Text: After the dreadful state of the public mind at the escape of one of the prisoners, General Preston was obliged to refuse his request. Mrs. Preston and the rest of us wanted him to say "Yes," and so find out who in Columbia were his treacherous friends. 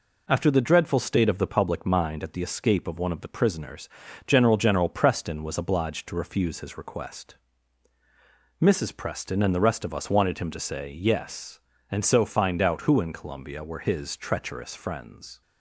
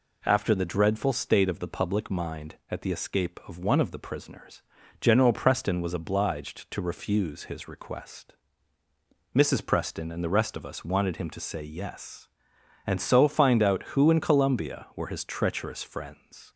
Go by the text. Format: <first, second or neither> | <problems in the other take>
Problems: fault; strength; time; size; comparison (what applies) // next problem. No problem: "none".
second | says "General" twice; at 4.5 s